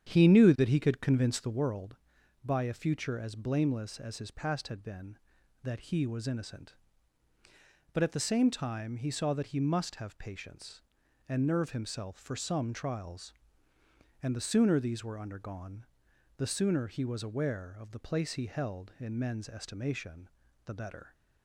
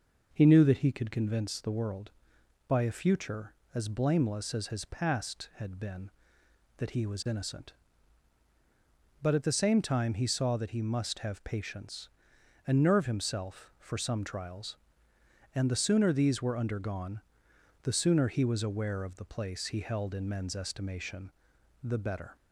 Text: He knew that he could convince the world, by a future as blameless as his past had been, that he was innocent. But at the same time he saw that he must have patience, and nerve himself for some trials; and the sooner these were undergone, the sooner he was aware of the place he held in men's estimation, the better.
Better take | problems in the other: second | starts louder than the rest; strong; until 1.6 s; 9 dB

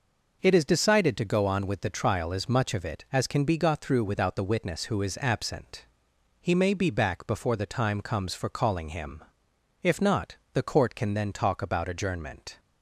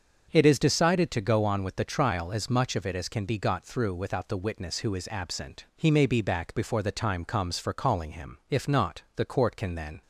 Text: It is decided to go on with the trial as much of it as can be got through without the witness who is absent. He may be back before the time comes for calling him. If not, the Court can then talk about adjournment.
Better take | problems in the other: first | starts louder than the rest; until 1.3 s; 7 dB // stops before "talk about adjournment"; at 10.0 s

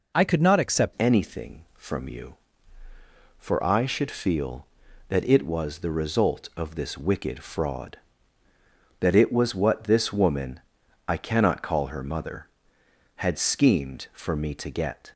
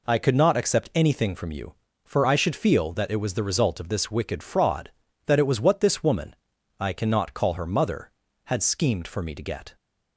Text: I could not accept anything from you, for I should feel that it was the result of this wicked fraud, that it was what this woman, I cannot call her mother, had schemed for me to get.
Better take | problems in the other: second | changes voice at "anything"; from 0.9 s on; 14.2 s long

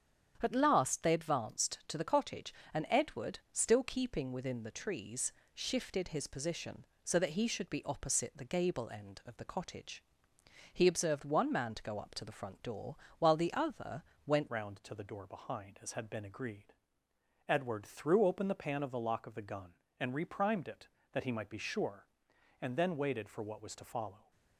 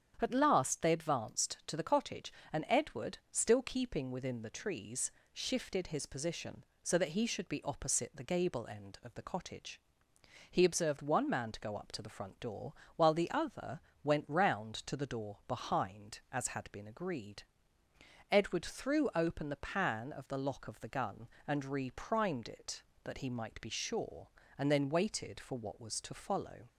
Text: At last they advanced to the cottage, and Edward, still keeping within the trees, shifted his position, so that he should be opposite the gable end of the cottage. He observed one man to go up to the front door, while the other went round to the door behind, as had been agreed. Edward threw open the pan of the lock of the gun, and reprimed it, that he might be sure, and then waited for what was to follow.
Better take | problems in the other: second | starts louder than the rest; strong; until 1.4 s; 8.5 dB; strong in the second // pauses between "other" and "went"; slight; at 14.0 s; 0.24 s long; slight in the second // changes voice at "round"; from 14.4 s on; 9.9 s long

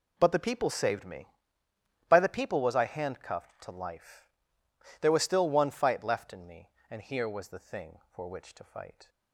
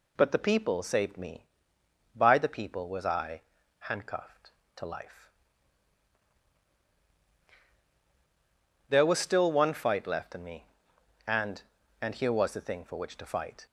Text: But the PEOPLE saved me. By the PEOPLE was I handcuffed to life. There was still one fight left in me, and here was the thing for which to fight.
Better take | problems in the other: first | pauses between "I" and "handcuffed"; at 3.4 s; 0.38 s long // says "and" twice; at 12.0 s

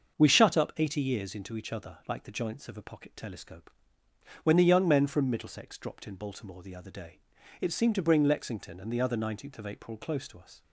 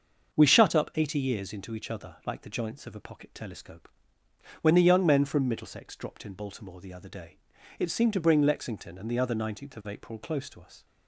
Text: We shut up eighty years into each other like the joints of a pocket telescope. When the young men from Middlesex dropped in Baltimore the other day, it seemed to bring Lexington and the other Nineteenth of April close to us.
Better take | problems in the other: neither | starts louder than the rest; the same in both

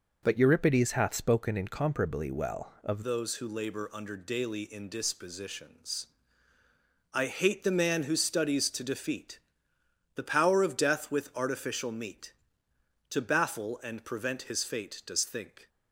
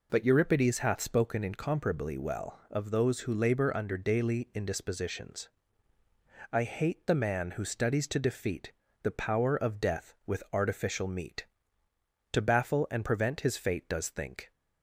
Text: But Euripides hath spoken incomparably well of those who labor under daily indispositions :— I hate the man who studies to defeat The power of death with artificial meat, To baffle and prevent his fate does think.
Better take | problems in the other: second | changes voice at "those"; from 3.0 s on; 12.6 s long // pauses between "defeat" and "The"; noticeable; at 9.3 s; 0.76 s long; slight in the second

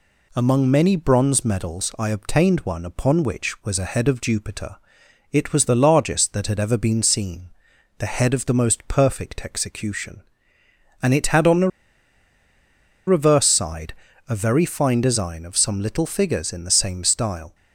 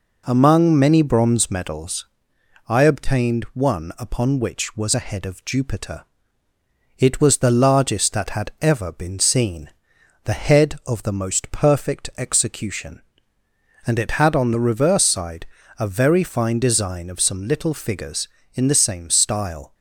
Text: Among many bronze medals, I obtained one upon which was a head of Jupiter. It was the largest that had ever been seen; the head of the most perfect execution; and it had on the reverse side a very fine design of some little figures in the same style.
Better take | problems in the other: second | pauses between "the" and "reverse"; strong; at 11.6 s; 1.3 s long // pauses between "side" and "a"; slight; at 13.9 s; 0.34 s long; slight in the second

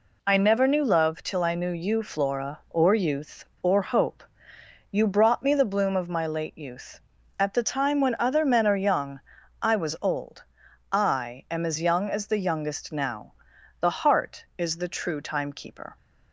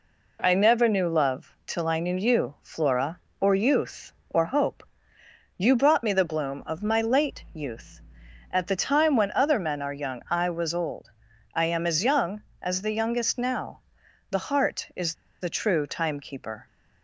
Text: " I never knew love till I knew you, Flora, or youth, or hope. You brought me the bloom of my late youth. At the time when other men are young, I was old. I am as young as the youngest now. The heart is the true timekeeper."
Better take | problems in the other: first | pauses between "is" and "the"; slight; at 15.1 s; 0.28 s long

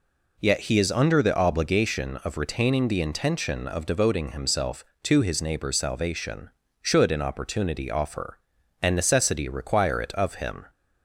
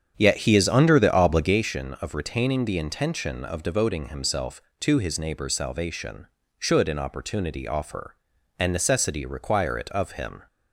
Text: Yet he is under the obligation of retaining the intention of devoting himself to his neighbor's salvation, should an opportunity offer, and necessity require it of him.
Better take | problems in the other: first | starts louder than the rest; strong; until 1.6 s; 8 dB

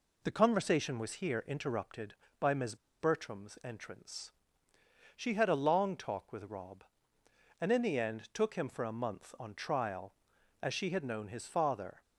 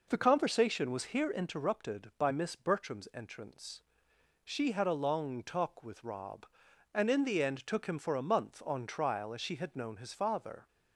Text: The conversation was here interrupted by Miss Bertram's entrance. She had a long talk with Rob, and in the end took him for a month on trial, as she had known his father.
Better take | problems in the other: second | pauses between "Miss" and "Bertram's"; slight; at 2.7 s; 0.24 s long

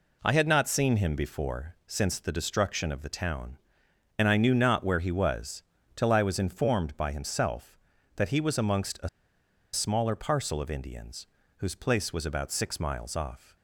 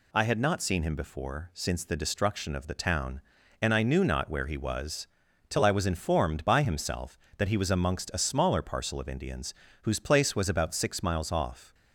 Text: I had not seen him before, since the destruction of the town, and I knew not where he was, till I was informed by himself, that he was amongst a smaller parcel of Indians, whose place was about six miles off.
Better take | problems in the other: second | pauses between "a" and "smaller"; noticeable; at 9.0 s; 0.66 s long

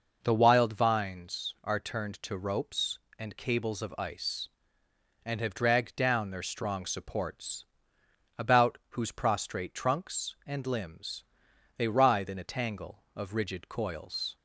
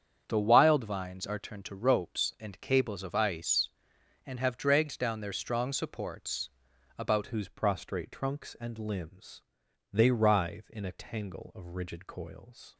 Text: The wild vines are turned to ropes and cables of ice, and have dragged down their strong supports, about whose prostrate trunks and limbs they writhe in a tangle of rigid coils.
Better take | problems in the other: first | starts louder than the rest; strong; until 1.2 s; 8 dB // changes voice at "whose"; from 7.2 s on; 5.5 s long // pauses between "limbs" and "they"; noticeable; at 9.4 s; 0.50 s long; noticeable in the first

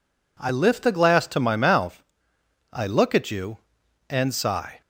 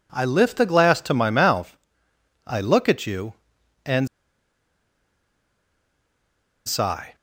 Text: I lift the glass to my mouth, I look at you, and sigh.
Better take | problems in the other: first | pauses between "and" and "sigh"; strong; at 4.0 s; 2.6 s long

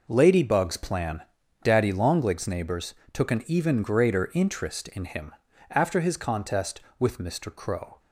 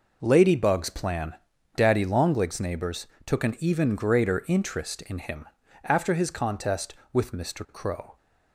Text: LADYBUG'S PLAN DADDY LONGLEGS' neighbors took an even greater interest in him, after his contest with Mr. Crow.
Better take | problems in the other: neither | pauses between "PLAN" and "DADDY"; the same in both // pauses between "neighbors" and "took"; slight; the same in both

